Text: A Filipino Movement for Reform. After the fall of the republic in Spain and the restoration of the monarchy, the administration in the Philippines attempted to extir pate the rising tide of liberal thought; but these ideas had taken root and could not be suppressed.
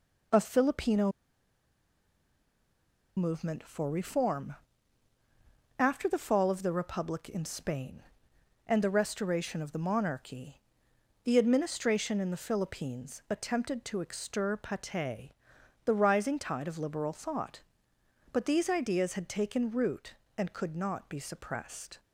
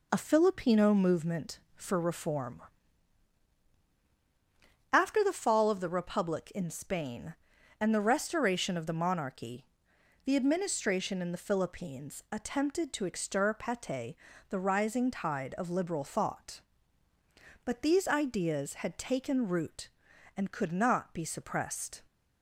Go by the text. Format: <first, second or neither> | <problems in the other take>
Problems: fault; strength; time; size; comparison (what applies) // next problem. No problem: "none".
second | pauses between "Filipino" and "Movement"; strong; at 1.1 s; 2.0 s long // pauses between "pate" and "the"; noticeable; at 15.3 s; 0.52 s long; slight in the second